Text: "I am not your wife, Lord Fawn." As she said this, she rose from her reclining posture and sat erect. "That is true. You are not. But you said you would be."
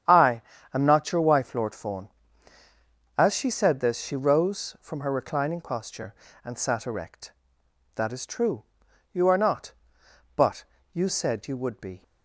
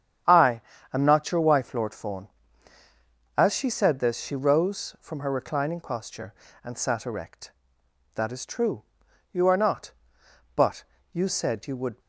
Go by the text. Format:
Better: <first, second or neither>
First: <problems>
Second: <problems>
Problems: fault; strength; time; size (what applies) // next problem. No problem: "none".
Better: first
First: starts louder than the rest; strong; until 1.4 s; 9.5 dB // pauses between "I" and "am"; slight; at 0.4 s; 0.32 s long // pauses between "But" and "you"; slight; at 10.6 s; 0.28 s long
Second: starts louder than the rest; strong; until 1.5 s; 9.5 dB // pauses between "I" and "am"; slight; at 0.6 s; 0.32 s long // pauses between "But" and "you"; slight; at 10.8 s; 0.28 s long // stops before "be"; at 12.0 s